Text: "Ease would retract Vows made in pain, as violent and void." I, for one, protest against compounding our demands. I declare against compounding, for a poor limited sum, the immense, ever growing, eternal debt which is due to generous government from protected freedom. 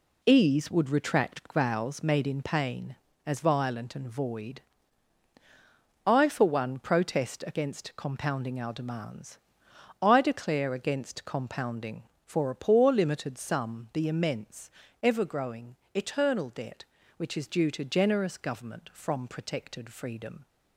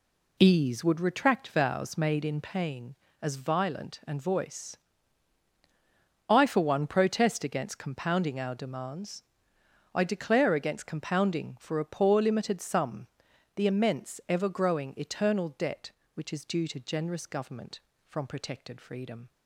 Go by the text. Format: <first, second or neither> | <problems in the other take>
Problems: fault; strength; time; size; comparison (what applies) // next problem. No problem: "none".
first | says "voice" for "void"; at 4.2 s